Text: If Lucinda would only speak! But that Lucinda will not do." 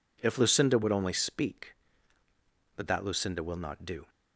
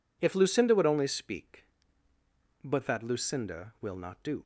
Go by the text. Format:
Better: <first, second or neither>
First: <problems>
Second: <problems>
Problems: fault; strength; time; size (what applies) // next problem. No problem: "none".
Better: neither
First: none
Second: none